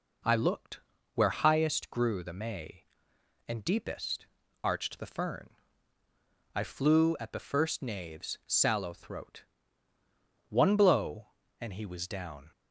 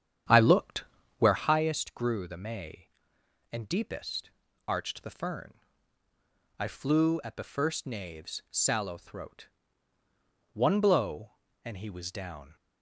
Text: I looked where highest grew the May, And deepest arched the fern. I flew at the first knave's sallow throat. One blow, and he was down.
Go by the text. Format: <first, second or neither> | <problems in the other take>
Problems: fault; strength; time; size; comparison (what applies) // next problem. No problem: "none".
first | starts louder than the rest; strong; until 1.4 s; 9 dB // pauses between "looked" and "where"; slight; at 0.8 s; 0.36 s long; slight in the first // pauses between "deepest" and "arched"; at 4.2 s; 0.38 s long; also in the first